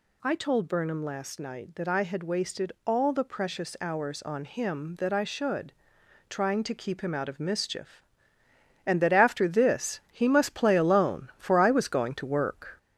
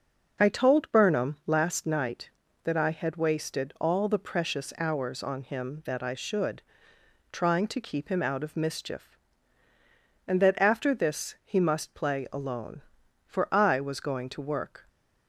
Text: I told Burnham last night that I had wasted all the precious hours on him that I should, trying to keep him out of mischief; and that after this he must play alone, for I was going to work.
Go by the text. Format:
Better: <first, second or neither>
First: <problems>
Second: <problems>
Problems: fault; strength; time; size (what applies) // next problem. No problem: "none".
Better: second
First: gets louder; slight; throughout; 3 dB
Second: none